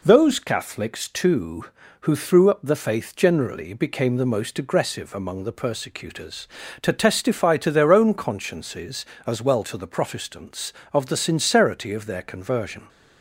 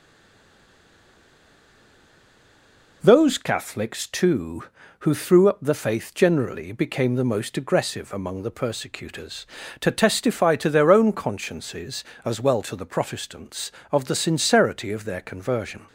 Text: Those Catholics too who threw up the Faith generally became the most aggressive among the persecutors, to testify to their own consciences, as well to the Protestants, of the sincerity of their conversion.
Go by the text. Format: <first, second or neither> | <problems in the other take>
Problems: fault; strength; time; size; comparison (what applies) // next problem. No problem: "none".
first | stays silent before the first word; strong; until 3.0 s; 3.0 s long